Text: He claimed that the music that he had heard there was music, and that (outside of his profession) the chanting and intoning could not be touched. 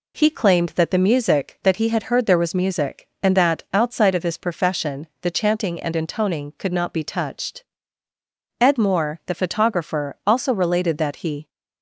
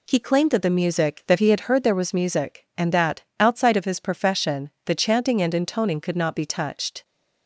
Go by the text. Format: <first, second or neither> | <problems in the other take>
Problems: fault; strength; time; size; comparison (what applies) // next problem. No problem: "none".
second | goes on to say "Ed Moore the photographer also related that he"; strong; from 8.6 s on; 2.8 s long